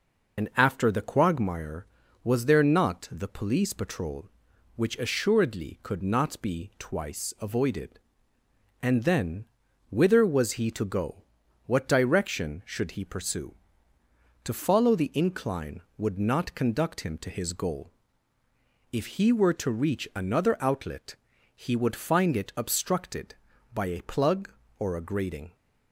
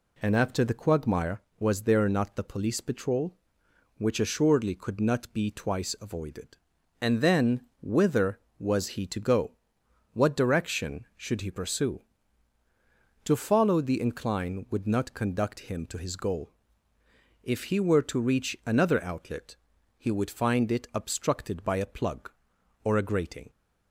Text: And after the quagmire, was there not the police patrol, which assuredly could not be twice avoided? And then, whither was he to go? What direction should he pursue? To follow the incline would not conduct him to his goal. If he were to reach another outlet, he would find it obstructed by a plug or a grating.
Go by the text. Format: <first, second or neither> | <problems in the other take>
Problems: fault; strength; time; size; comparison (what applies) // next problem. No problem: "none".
second | loses the start of "And"; at 0.3 s; 100 ms